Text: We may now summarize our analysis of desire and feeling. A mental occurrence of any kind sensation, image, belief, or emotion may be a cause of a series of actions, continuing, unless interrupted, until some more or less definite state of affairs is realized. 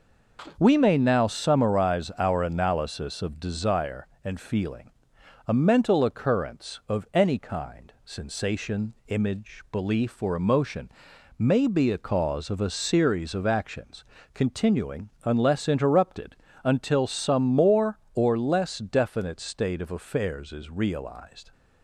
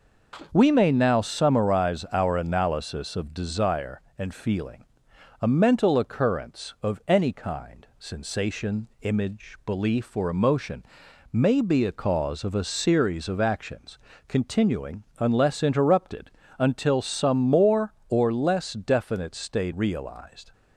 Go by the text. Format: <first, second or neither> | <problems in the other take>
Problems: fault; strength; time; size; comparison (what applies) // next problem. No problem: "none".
first | pauses between "emotion" and "may"; noticeable; at 10.8 s; 0.48 s long; noticeable in the first // skips "of affairs is"; at 19.7 s